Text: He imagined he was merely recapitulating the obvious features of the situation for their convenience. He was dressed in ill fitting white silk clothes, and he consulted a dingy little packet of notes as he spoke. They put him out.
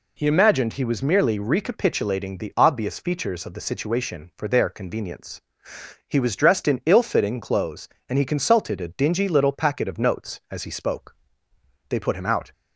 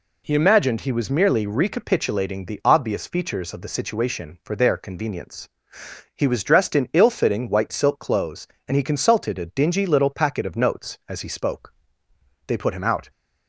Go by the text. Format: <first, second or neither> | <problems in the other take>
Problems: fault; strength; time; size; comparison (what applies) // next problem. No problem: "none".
second | skips "white silk"; at 7.3 s